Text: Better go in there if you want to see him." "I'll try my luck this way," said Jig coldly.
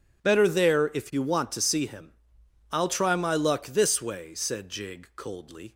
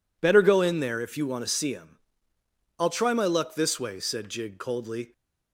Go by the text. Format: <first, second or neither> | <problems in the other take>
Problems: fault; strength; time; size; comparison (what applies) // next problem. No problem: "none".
second | skips "go in"; at 0.4 s